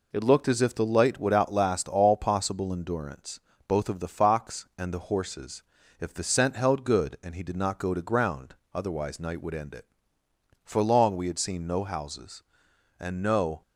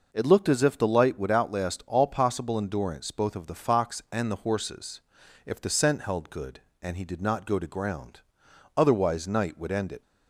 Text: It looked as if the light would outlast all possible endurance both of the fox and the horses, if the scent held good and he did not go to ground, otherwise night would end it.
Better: second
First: pauses between "endurance" and "both"; slight; at 3.3 s; 0.28 s long // goes on to say "For long we had seen no houses and no"; strong; from 10.6 s on; 2.9 s long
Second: none

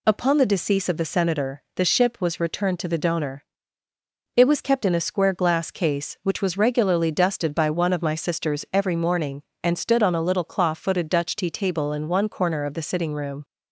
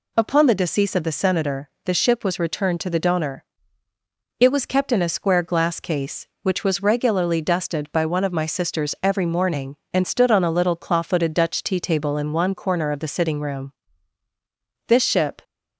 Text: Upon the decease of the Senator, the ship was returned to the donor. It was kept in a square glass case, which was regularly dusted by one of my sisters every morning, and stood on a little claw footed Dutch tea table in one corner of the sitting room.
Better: first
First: none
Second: goes on to say "This ship"; from 14.8 s on; 0.56 s long

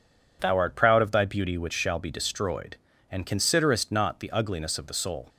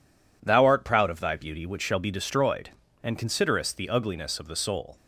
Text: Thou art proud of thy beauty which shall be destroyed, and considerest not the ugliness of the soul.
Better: first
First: none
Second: skips "not"; at 3.7 s

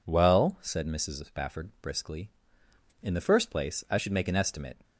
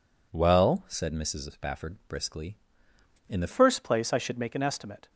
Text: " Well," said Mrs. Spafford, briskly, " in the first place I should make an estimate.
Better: first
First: none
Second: changes voice at "first"; from 3.5 s on; 1.5 s long

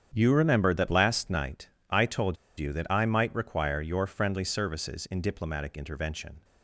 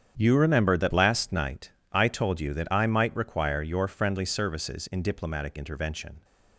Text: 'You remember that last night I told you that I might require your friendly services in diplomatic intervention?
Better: second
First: starts louder than the rest; strong; until 1.1 s; 8.5 dB // pauses between "night" and "I"; slight; at 1.6 s; 0.20 s long // pauses between "told" and "you"; slight; at 2.3 s; 0.22 s long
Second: starts louder than the rest; strong; until 1.1 s; 8.5 dB // pauses between "night" and "I"; slight; at 1.7 s; 0.20 s long

